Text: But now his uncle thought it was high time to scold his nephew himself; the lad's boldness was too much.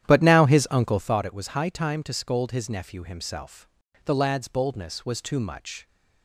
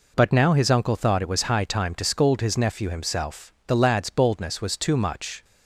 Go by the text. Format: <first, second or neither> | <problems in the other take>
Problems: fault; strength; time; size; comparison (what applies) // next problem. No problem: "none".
second | starts louder than the rest; strong; until 1.3 s; 11 dB